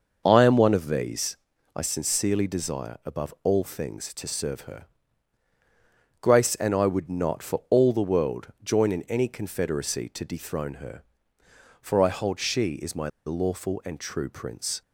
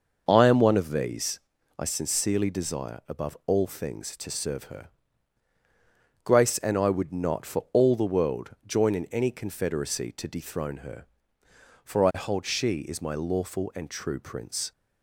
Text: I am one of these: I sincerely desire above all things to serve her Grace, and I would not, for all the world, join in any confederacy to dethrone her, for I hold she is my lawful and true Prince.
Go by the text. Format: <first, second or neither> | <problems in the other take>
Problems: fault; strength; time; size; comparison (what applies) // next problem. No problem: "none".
second | starts louder than the rest; noticeable; until 1.2 s; 6 dB; noticeable in the second // pauses between "her" and "Grace"; strong; at 4.8 s; 1.3 s long; strong in the second // pauses between "my" and "lawful"; slight; at 13.0 s; 0.16 s long